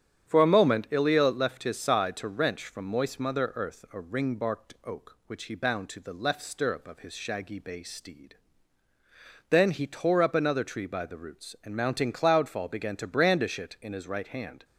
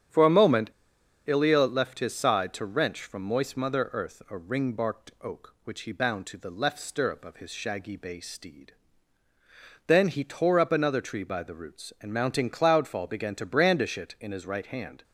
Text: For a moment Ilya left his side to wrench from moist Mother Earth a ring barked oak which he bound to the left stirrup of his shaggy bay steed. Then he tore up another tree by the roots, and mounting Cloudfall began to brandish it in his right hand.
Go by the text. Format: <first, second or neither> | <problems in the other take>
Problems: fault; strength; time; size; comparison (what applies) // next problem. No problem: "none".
first | starts louder than the rest; strong; until 1.6 s; 9 dB; strong in the first // pauses between "moment" and "Ilya"; noticeable; at 0.7 s; 0.56 s long